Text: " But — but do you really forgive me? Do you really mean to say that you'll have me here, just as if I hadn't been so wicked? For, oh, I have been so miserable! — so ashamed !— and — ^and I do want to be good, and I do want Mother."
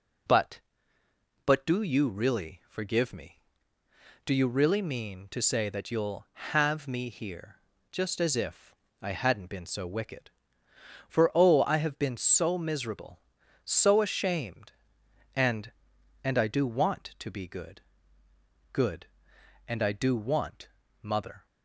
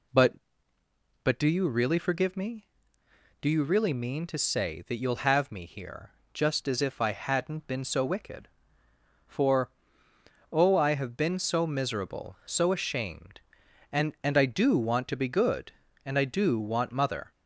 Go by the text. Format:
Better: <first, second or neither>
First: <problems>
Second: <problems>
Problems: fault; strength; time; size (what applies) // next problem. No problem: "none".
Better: second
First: pauses between "if" and "I"; slight; at 8.7 s; 0.26 s long // says "good" twice; at 18.7 s // pauses between "want" and "Mother"; slight; at 20.6 s; 0.34 s long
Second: none